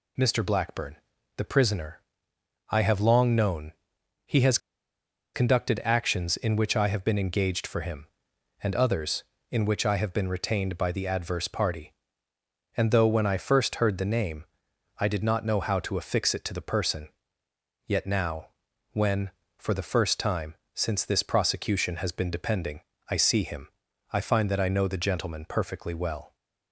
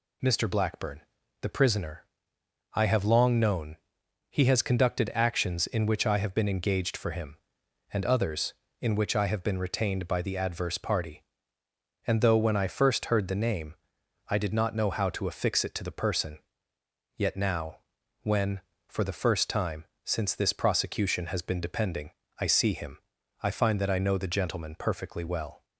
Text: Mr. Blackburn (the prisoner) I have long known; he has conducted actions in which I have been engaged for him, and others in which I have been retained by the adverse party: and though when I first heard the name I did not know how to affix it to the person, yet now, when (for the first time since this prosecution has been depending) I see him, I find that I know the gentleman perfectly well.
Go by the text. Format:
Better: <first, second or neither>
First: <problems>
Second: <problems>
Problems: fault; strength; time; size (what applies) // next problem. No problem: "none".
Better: second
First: pauses between "has" and "conducted"; noticeable; at 4.5 s; 0.77 s long // pauses between "name" and "I"; noticeable; at 14.4 s; 0.54 s long // pauses between "time" and "since"; slight; at 20.5 s; 0.22 s long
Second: pauses between "name" and "I"; noticeable; at 13.7 s; 0.54 s long // pauses between "time" and "since"; slight; at 19.8 s; 0.22 s long